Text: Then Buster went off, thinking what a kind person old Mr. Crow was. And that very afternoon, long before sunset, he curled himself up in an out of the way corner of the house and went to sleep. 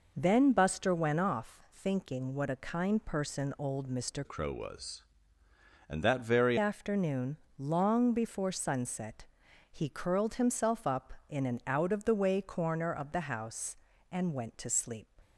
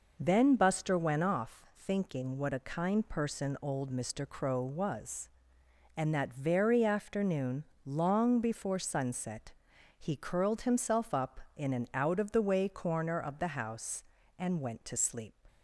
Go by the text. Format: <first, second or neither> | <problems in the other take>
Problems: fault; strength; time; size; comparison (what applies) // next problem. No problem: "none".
second | changes voice from "Crow" to "very"; from 4.2 to 6.5 s; 2.3 s long